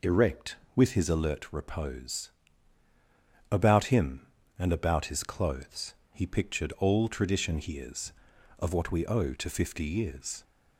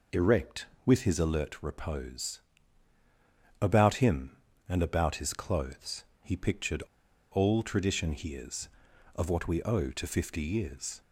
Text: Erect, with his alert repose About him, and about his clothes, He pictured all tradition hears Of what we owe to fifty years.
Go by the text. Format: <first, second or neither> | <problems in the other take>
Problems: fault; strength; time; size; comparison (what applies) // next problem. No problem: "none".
first | pauses between "repose" and "About"; at 2.4 s; 1.2 s long; also in the first // pauses between "pictured" and "all"; noticeable; at 6.8 s; 0.50 s long